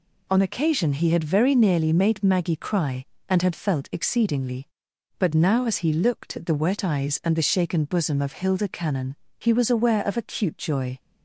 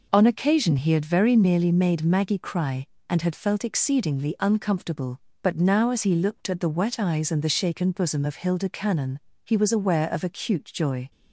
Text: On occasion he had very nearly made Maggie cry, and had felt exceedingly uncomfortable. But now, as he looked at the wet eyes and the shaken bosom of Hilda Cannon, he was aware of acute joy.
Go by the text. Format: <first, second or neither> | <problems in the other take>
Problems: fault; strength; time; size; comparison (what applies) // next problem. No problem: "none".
second | skips "uncomfortable"; at 4.9 s